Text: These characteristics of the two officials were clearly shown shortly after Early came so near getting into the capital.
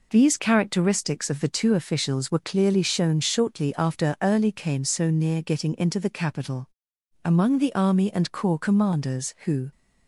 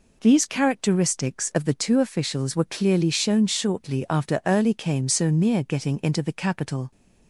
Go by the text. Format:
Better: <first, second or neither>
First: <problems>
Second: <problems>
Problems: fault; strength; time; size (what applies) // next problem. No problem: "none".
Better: second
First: goes on to say "Among the army and corps commanders who"; strong; from 7.2 s on; 2.4 s long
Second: none